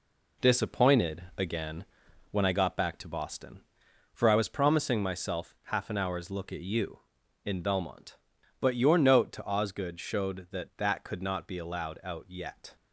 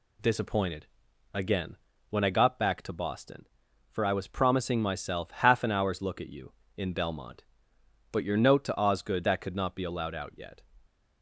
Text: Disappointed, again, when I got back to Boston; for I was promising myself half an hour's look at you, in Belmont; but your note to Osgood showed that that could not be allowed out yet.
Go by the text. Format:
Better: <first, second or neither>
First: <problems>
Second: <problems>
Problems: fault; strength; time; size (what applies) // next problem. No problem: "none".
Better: first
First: none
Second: skips "showed that"; at 9.2 s